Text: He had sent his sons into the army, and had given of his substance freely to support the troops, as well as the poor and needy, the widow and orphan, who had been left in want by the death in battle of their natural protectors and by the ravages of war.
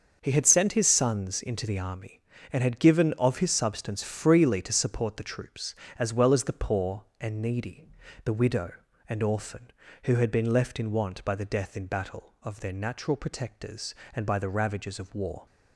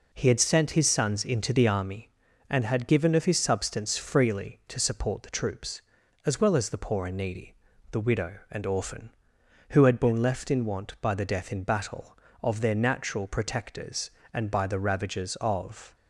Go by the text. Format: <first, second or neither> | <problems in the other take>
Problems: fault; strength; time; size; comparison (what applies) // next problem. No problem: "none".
first | stops before "war"; at 15.9 s